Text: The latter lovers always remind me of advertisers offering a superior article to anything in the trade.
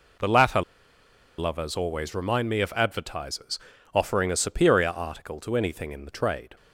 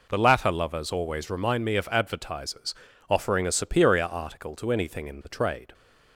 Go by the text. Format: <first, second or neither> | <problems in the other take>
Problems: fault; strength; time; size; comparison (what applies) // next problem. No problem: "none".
second | pauses between "latter" and "lovers"; noticeable; at 0.6 s; 0.76 s long // pauses between "advertisers" and "offering"; slight; at 3.5 s; 0.36 s long; slight in the second